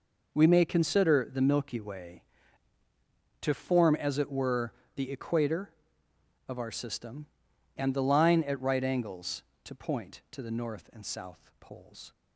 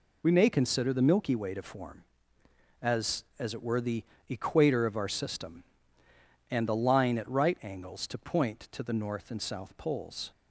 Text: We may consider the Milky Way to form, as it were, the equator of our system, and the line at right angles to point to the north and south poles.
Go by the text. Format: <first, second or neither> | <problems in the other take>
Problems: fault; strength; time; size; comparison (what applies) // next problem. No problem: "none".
first | says "as" twice; at 3.3 s // pauses between "the" and "equator"; slight; at 4.0 s; 0.26 s long